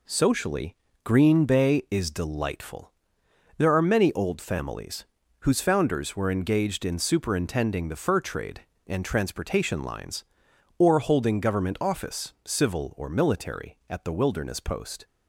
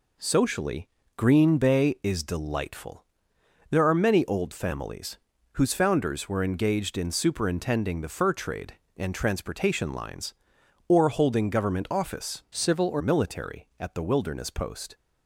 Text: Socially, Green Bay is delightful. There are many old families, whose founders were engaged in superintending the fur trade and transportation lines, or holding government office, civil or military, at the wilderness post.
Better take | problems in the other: first | changes voice from "civil" to "or"; from 12.5 to 13.0 s; 0.5 s long

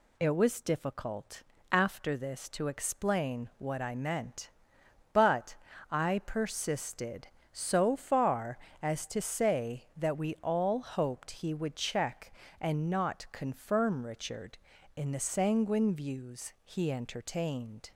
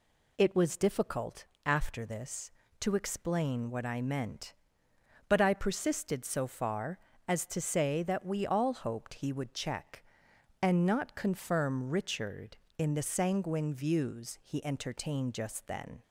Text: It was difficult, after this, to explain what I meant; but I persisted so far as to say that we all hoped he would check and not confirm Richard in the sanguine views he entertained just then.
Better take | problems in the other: second | pauses between "but" and "I"; slight; at 5.5 s; 0.34 s long // stops before "just then"; at 17.9 s

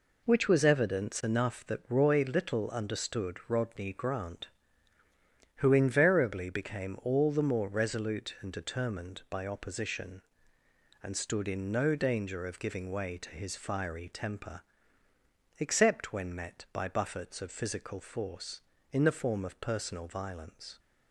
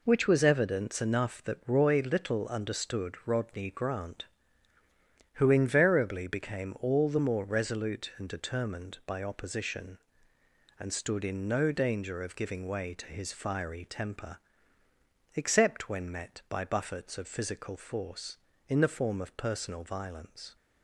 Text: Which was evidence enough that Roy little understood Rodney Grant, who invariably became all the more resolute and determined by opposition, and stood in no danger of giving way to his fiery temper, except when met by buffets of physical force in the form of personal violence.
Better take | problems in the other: neither | none

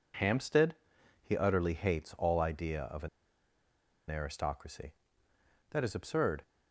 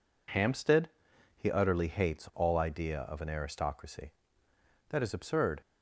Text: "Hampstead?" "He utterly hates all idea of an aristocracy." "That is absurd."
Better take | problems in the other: second | pauses between "an" and "aristocracy"; at 3.0 s; 1.0 s long

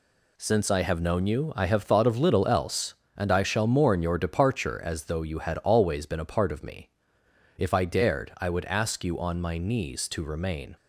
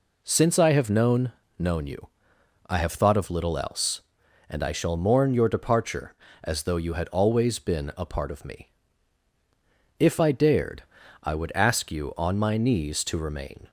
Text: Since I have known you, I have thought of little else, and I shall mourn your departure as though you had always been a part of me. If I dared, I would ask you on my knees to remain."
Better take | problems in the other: first | says "known" twice; at 1.5 s

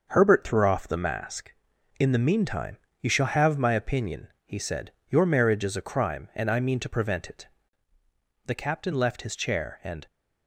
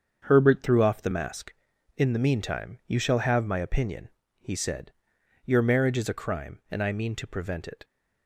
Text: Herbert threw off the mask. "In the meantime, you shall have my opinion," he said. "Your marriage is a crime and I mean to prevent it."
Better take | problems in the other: second | starts louder than the rest; until 1.1 s; 6.5 dB; strong in the second // goes on to say "The Captain left his chair and"; from 8.4 s on; 1.6 s long

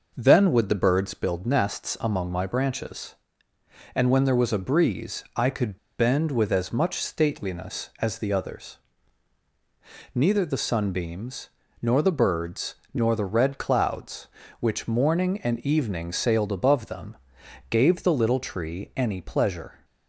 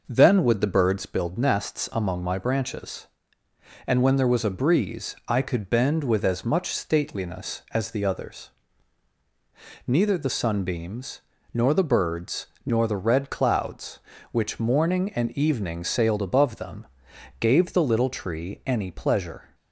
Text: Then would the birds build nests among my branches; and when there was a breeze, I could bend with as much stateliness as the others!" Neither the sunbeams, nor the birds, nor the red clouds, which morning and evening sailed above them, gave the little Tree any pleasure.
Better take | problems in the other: second | pauses between "could" and "bend"; slight; at 5.7 s; 0.19 s long

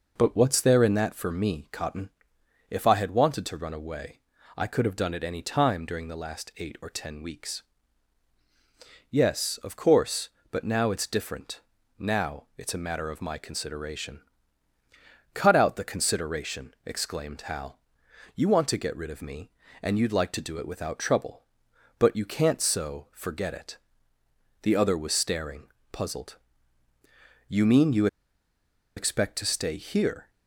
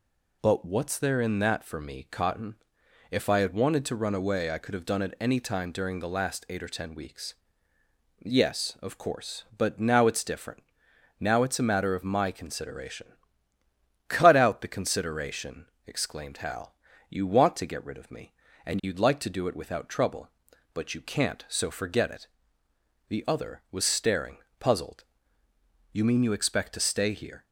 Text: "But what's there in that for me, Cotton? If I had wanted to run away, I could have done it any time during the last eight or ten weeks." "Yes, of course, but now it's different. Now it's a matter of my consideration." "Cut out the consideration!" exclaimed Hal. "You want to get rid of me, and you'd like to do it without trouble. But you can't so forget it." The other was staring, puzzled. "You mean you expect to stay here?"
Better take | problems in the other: second | pauses between "you" and "expect"; noticeable; at 28.0 s; 0.90 s long

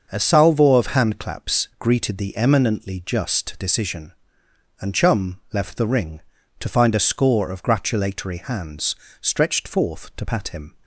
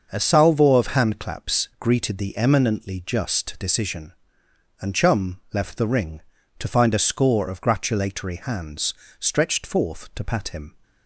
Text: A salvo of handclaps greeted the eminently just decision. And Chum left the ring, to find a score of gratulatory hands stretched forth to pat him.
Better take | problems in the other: neither | starts louder than the rest; the same in both // pauses between "hands" and "stretched"; slight; the same in both

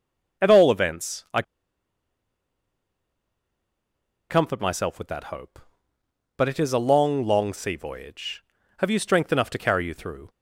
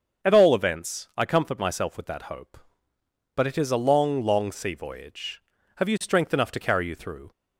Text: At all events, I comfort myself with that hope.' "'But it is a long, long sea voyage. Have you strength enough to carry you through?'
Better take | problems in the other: second | starts louder than the rest; until 4.3 s; 7 dB; also in the second // pauses between "I" and "comfort"; strong; at 1.4 s; 2.8 s long

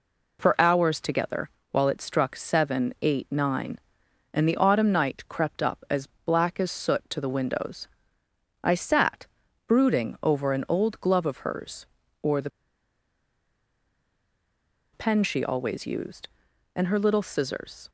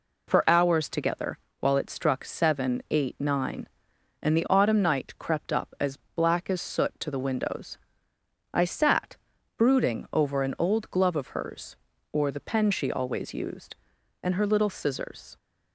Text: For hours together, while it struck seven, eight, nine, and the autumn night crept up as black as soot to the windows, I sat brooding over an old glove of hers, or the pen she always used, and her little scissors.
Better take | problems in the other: second | pauses between "as" and "black"; slight; at 6.0 s; 0.16 s long; slight in the second // pauses between "sat" and "brooding"; at 9.2 s; 0.42 s long; also in the second // pauses between "the" and "pen"; strong; at 12.4 s; 2.4 s long

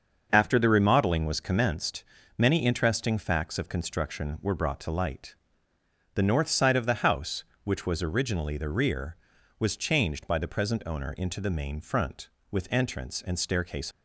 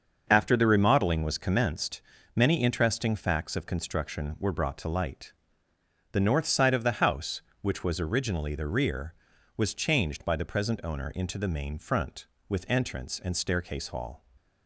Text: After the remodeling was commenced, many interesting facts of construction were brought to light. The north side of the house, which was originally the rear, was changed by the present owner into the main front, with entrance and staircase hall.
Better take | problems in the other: second | starts louder than the rest; until 1.3 s; 6.5 dB; also in the second // stops before "hall"; at 13.9 s

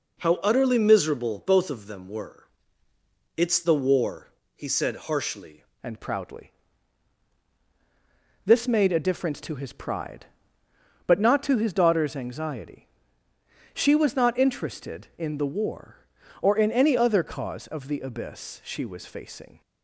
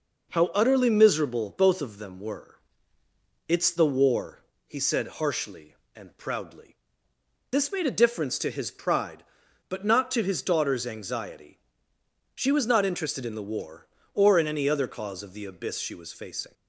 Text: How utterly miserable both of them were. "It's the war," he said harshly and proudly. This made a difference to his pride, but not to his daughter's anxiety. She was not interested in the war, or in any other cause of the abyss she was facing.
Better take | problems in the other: second | changes voice at "and"; from 5.8 s on; 13.8 s long

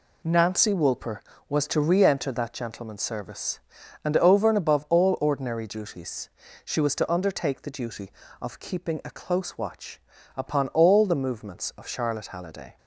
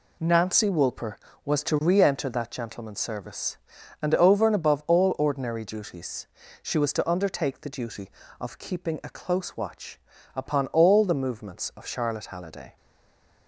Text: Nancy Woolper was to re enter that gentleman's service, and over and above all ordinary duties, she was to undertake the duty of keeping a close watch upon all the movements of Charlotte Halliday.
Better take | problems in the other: first | pauses between "watch" and "upon"; slight; at 10.0 s; 0.34 s long; slight in the first // stays silent after the last word; slight; from 12.7 s on; 0.7 s long

